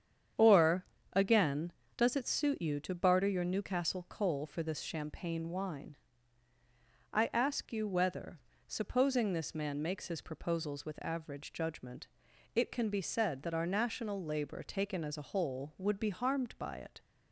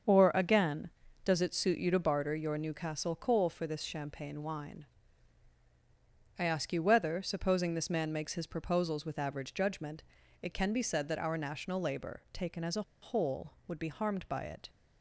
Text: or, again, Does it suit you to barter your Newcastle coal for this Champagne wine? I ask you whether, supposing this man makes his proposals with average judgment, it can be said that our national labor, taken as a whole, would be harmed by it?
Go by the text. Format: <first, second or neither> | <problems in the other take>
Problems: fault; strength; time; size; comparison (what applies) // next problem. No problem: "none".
first | starts louder than the rest; until 1.4 s; 7 dB; strong in the first // pauses between "a" and "whole"; slight; at 12.8 s; 0.20 s long